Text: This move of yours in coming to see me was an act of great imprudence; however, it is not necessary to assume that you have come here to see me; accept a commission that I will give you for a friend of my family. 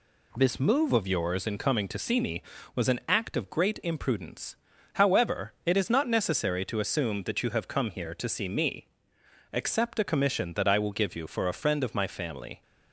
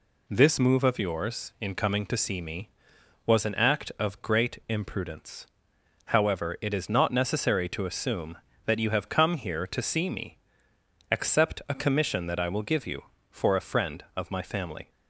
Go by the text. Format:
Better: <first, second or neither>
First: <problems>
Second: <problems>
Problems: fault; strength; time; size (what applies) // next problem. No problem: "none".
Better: neither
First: none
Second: none